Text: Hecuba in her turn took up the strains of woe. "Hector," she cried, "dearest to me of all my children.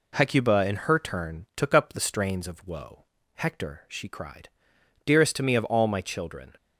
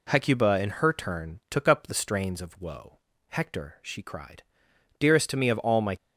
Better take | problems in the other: first | stops before "children"; at 5.9 s

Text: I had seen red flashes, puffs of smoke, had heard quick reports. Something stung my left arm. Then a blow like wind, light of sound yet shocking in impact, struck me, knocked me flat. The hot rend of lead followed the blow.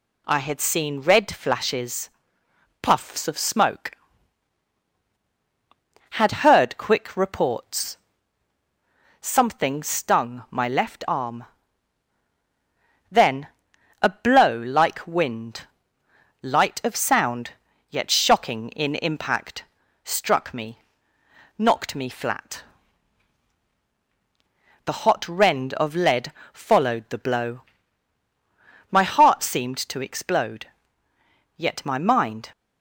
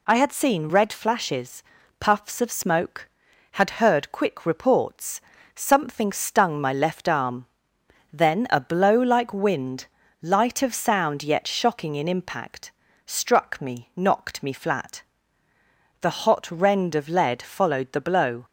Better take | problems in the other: second | pauses between "Then" and "a"; noticeable; at 13.4 s; 0.52 s long // pauses between "sound" and "yet"; at 17.5 s; 0.40 s long // pauses between "lead" and "followed"; slight; at 26.3 s; 0.20 s long // goes on to say "My heart seemed to explode yet my mind"; strong; from 28.9 s on; 3.6 s long

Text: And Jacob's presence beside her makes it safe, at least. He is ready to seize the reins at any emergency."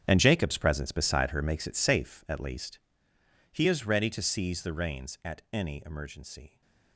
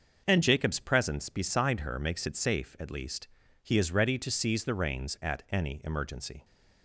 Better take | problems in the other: second | gets quieter; strong; throughout; 15 dB // starts louder than the rest; strong; until 1.1 s; 8.5 dB; noticeable in the second

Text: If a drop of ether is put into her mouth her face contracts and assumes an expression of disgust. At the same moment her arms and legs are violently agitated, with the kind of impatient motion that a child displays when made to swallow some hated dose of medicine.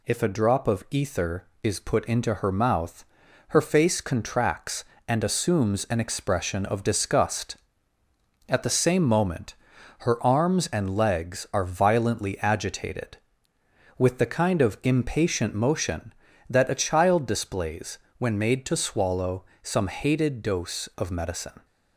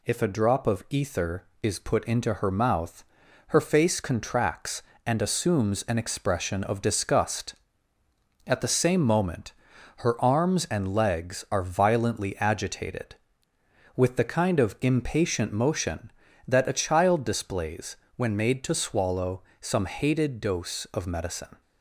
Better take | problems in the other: neither | pauses between "mouth" and "her"; the same in both // pauses between "moment" and "her"; noticeable; the same in both // pauses between "displays" and "when"; slight; the same in both // pauses between "swallow" and "some"; slight; the same in both

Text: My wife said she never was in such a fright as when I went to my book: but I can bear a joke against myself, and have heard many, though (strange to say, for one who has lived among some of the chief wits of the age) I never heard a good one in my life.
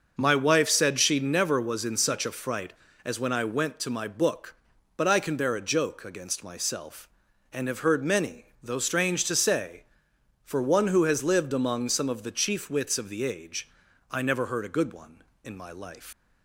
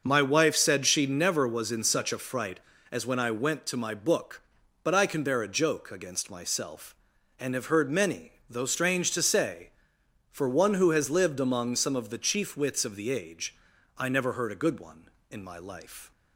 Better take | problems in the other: second | leaves "life" unfinished; at 16.1 s; 115 ms

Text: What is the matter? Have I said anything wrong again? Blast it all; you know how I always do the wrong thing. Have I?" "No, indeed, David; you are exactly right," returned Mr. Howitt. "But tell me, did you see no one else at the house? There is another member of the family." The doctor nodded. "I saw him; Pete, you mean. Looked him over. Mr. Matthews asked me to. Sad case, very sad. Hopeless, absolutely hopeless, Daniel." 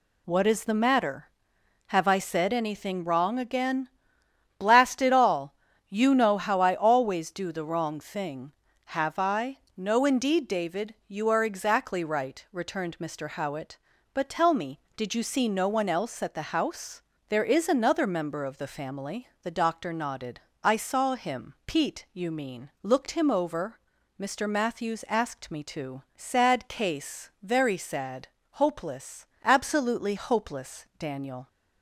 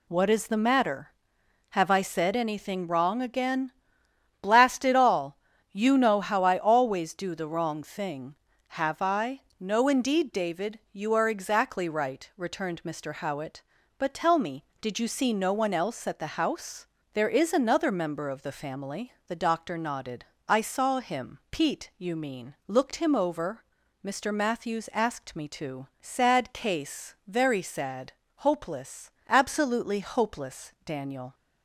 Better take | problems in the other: neither | none

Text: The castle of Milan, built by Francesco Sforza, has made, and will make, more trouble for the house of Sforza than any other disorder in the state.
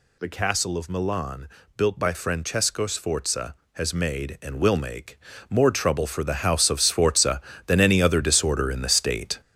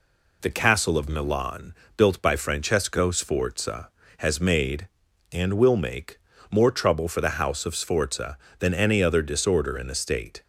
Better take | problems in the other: second | gets louder; throughout; 7 dB

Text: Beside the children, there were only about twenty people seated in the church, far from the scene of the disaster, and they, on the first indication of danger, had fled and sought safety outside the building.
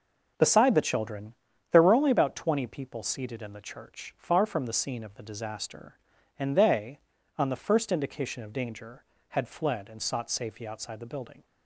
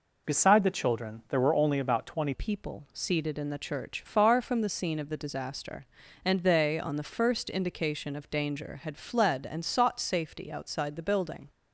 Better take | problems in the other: first | changes voice at "people"; from 2.3 s on; 9.1 s long

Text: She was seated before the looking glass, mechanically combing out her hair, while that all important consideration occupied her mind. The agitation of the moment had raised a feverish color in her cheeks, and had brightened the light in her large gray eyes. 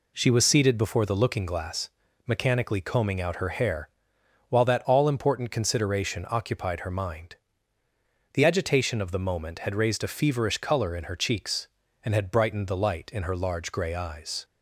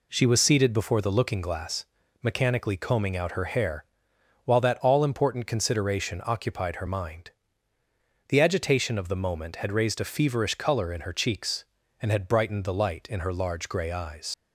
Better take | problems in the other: first | leaves "eyes" unfinished; at 14.3 s; 75 ms

